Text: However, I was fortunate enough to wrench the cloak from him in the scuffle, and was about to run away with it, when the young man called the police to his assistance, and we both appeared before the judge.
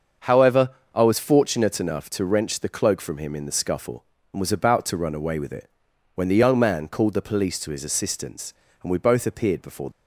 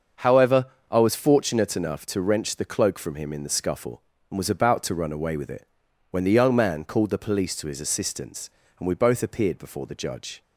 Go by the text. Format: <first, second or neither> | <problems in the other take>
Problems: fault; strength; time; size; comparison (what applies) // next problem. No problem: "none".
second | starts louder than the rest; until 1.4 s; 6.5 dB; also in the second // stops before "the judge"; at 9.9 s